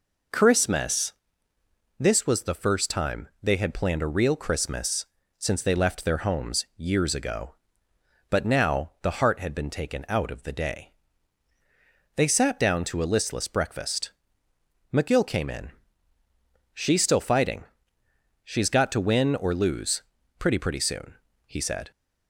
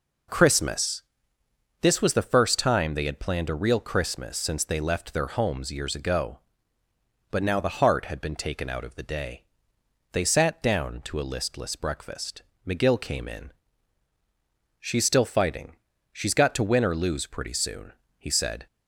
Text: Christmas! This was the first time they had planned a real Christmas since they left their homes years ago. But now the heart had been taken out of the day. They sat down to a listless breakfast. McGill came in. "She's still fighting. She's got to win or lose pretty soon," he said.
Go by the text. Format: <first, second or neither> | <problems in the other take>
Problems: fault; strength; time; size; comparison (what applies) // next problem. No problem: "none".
second | pauses between "Christmas" and "since"; slight; at 5.0 s; 0.32 s long // pauses between "lose" and "pretty"; at 20.0 s; 0.38 s long // says "pretty" twice; at 20.5 s